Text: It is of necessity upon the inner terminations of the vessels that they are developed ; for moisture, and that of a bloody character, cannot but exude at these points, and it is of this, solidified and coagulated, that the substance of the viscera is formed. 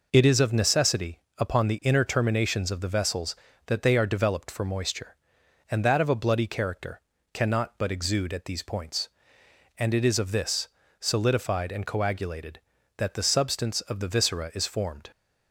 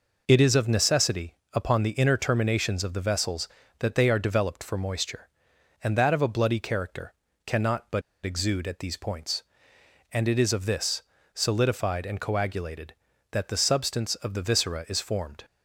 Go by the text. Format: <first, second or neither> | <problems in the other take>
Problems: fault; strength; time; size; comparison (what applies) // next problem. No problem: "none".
first | pauses between "necessity" and "upon"; slight; at 1.3 s; 0.18 s long; slight in the first // pauses between "but" and "exude"; slight; at 8.0 s; 0.23 s long